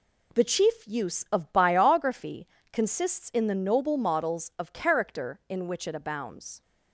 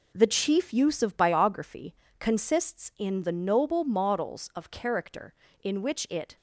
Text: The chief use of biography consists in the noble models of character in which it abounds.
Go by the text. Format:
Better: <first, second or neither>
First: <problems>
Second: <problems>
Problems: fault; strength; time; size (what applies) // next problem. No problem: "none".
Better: first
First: pauses between "biography" and "consists"; slight; at 2.4 s; 0.24 s long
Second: pauses between "biography" and "consists"; slight; at 1.9 s; 0.24 s long // stops before "abounds"; at 6.3 s